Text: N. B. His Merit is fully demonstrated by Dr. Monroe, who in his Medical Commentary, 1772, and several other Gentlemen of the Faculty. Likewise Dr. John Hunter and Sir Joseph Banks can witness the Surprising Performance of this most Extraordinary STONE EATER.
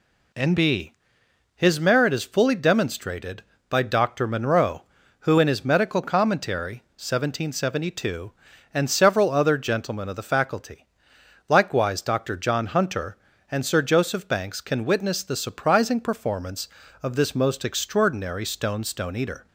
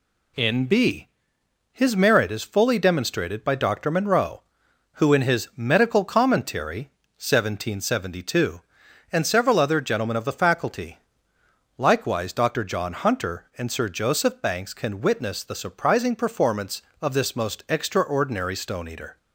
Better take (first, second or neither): second